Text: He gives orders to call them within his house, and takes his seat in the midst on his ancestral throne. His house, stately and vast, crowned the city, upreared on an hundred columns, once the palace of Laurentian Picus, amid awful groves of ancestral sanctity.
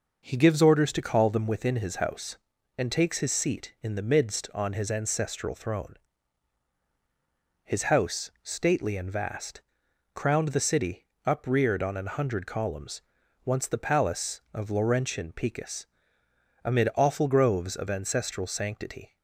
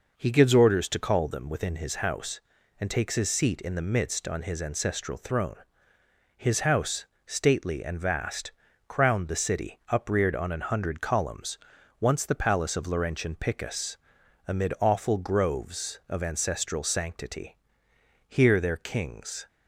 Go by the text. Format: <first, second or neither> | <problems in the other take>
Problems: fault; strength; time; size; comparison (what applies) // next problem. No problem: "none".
first | goes on to say "Here their kings"; noticeable; from 18.2 s on; 1.2 s long